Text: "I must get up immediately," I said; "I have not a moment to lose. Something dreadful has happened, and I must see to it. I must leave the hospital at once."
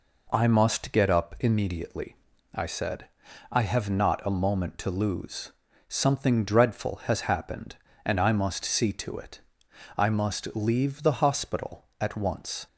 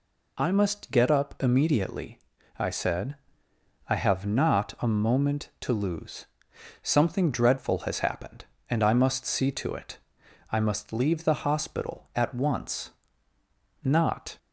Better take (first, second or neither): first